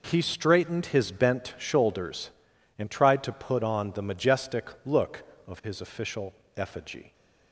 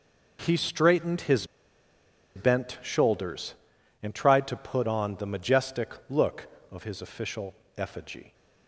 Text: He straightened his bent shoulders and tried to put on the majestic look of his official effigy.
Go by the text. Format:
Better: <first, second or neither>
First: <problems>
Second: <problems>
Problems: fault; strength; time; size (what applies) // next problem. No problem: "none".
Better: first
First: pauses between "majestic" and "look"; slight; at 4.6 s; 0.16 s long // pauses between "official" and "effigy"; slight; at 6.3 s; 0.24 s long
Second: pauses between "his" and "bent"; noticeable; at 1.4 s; 0.89 s long // pauses between "majestic" and "look"; slight; at 5.9 s; 0.16 s long // pauses between "official" and "effigy"; slight; at 7.5 s; 0.24 s long